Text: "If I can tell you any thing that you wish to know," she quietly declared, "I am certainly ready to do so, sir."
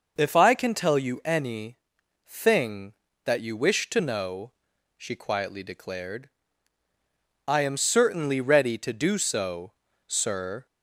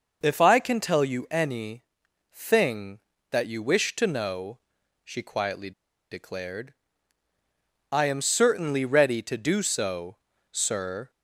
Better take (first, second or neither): first